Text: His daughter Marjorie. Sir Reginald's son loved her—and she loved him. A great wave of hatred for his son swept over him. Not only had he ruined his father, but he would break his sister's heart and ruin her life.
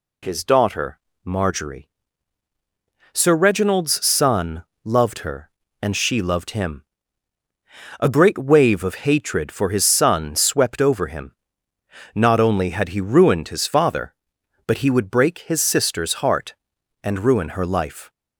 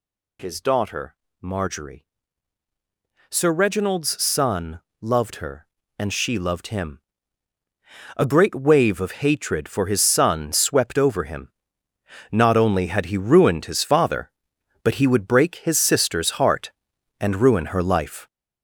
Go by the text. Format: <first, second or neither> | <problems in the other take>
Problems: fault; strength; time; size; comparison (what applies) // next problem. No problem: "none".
first | gets louder; throughout; 7 dB // pauses between "daughter" and "Marjorie"; slight; at 1.1 s; 0.28 s long; slight in the first // pauses between "son" and "loved"; slight; at 4.8 s; 0.18 s long; slight in the first